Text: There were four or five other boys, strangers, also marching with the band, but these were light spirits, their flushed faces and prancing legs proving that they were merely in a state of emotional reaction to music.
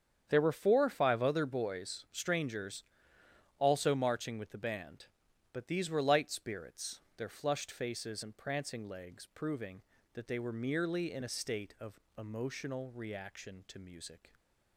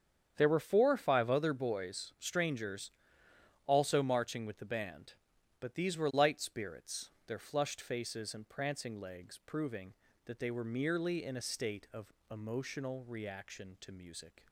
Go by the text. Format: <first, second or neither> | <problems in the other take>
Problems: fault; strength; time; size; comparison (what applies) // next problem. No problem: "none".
neither | starts louder than the rest; strong; the same in both // pauses between "of" and "emotional"; slight; the same in both